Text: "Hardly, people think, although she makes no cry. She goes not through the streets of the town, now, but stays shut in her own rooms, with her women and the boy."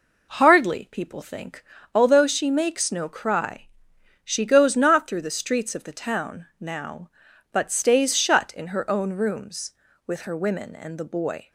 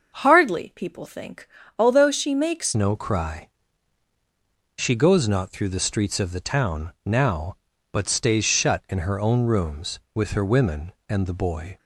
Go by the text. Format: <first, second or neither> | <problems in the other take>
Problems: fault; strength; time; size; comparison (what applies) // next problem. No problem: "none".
first | starts louder than the rest; until 1.1 s; 6.5 dB // changes voice at "no"; from 2.7 s on; 9.0 s long